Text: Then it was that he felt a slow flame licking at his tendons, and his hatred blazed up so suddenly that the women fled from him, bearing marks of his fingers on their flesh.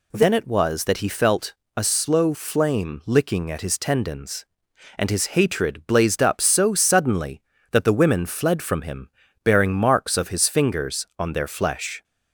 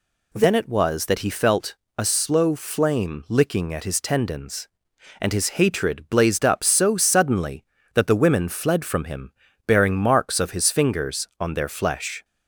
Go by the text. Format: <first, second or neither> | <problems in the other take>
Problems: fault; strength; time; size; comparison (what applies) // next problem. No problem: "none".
neither | pauses between "felt" and "a"; slight; the same in both